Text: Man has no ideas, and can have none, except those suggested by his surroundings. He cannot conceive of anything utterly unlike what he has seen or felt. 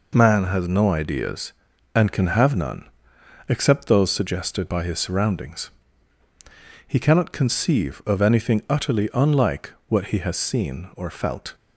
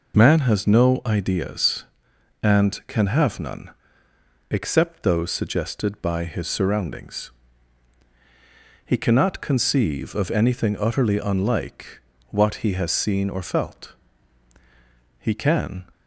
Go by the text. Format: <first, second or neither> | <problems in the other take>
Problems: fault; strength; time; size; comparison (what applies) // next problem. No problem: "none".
first | pauses between "unlike" and "what"; slight; at 12.0 s; 0.28 s long; slight in the first // goes on to say "He can"; noticeable; from 15.1 s on; 0.68 s long